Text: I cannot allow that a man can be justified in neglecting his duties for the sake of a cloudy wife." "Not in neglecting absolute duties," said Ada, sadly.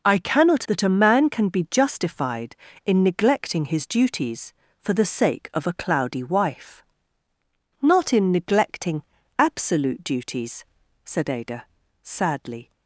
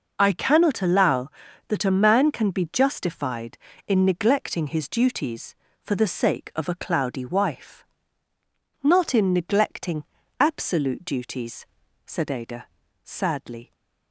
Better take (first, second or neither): second